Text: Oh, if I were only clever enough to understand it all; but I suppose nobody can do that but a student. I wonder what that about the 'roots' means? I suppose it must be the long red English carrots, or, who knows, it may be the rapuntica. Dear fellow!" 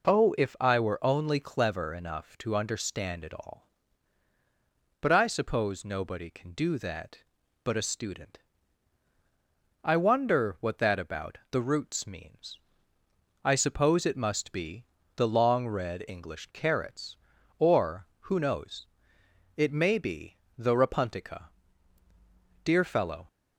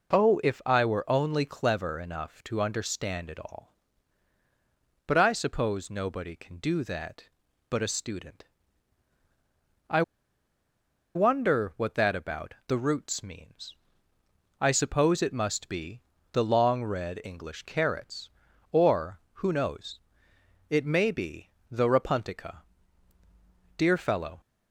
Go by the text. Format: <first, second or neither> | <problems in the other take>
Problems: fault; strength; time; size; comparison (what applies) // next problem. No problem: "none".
first | pauses between "I" and "wonder"; at 10.0 s; 1.1 s long // pauses between "be" and "the"; slight; at 16.0 s; 0.30 s long; slight in the first // pauses between "be" and "the"; slight; at 21.5 s; 0.20 s long; slight in the first